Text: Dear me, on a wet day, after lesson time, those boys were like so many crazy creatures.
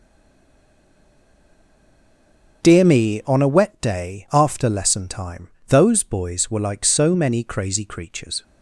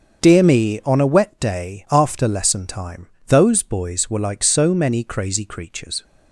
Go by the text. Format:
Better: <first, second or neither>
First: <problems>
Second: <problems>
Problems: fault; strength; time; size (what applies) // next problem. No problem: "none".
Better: second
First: stays silent before the first word; strong; until 2.6 s; 2.6 s long // starts louder than the rest; strong; until 3.6 s; 7.5 dB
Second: starts louder than the rest; strong; until 1.2 s; 7.5 dB